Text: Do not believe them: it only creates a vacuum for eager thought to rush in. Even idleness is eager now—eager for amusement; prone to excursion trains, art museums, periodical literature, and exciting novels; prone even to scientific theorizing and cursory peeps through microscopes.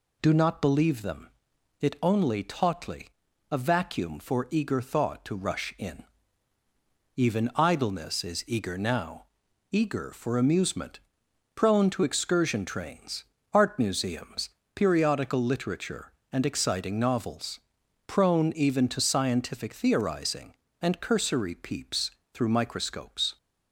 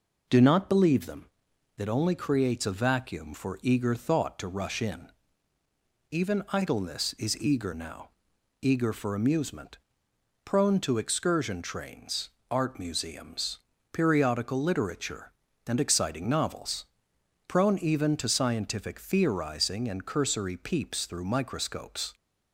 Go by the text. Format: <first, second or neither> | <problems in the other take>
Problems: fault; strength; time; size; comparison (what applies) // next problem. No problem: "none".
second | says "tautly" for "creates"; at 2.4 s // pauses between "peeps" and "through"; slight; at 22.0 s; 0.24 s long